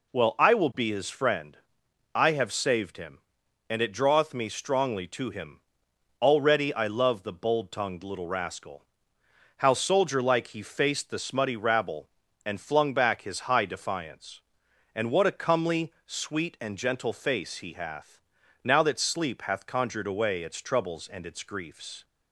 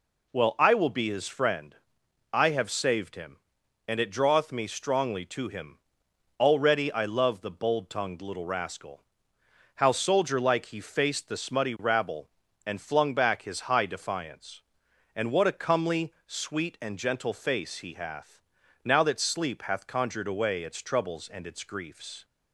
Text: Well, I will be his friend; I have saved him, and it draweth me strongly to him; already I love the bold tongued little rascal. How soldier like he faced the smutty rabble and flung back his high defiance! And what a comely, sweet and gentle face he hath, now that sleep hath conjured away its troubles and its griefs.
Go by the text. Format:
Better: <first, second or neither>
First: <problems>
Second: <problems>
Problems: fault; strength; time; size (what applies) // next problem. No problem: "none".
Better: neither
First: none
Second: none